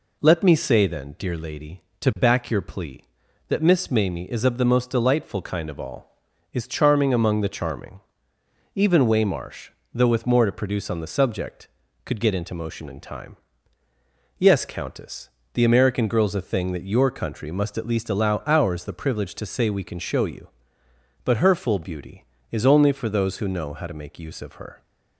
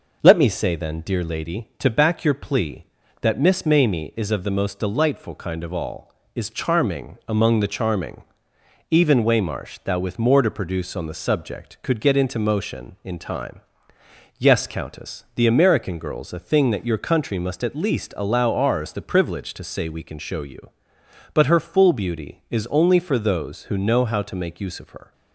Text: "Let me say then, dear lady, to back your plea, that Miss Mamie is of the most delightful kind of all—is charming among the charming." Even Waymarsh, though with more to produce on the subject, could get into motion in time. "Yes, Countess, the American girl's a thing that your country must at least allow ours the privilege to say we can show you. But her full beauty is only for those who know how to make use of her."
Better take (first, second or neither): first